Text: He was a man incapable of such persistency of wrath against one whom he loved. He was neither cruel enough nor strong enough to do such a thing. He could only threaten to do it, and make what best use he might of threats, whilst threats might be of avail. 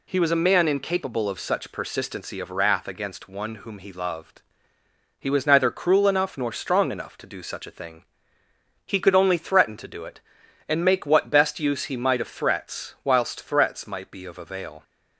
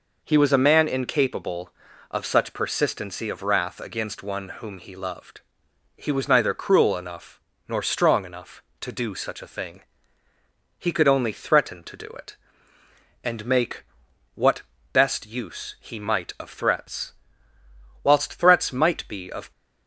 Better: first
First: none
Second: pauses between "enough" and "nor"; slight; at 7.3 s; 0.28 s long // pauses between "make" and "what"; noticeable; at 13.8 s; 0.52 s long // pauses between "what" and "best"; slight; at 14.6 s; 0.30 s long // stops before "avail"; at 19.5 s

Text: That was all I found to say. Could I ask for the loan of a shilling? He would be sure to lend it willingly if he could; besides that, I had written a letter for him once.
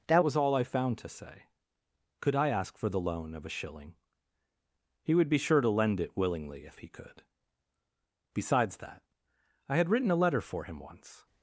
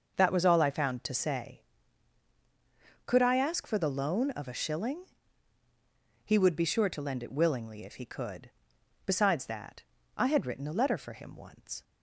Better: second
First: changes voice at "was"; from 0.2 s on; 11.0 s long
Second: none

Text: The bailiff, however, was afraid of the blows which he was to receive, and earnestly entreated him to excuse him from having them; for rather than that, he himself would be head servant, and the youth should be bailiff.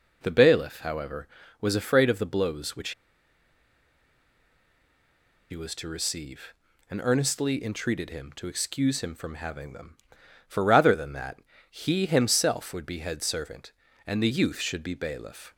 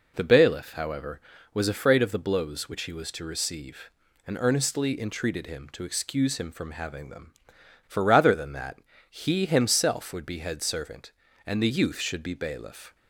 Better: second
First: pauses between "which" and "he"; strong; at 2.9 s; 2.5 s long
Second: none

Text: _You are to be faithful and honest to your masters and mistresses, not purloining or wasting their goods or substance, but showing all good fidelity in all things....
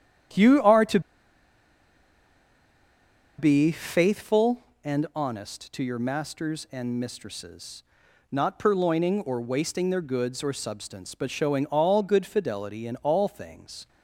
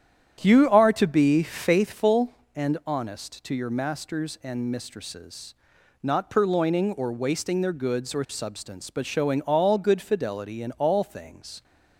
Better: second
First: starts louder than the rest; strong; until 3.7 s; 9.5 dB // pauses between "to" and "be"; strong; at 0.9 s; 2.3 s long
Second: starts louder than the rest; strong; until 1.4 s; 9.5 dB

